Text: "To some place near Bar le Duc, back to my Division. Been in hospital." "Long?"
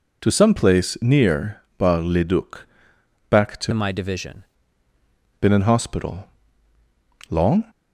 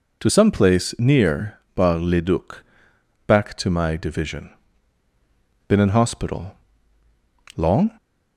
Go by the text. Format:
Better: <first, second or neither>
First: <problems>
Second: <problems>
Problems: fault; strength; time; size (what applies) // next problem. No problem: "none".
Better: second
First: pauses between "near" and "Bar"; slight; at 1.6 s; 0.18 s long // changes voice from "my" to "Division"; from 3.7 to 4.4 s; 0.7 s long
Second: pauses between "near" and "Bar"; slight; at 1.5 s; 0.18 s long